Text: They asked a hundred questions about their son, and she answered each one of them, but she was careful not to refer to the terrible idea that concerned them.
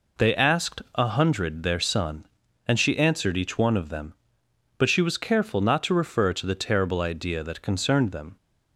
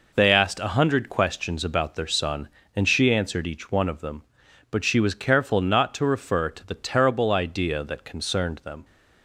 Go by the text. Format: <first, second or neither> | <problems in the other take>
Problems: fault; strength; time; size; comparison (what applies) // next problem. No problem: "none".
second | skips "questions about"; at 1.6 s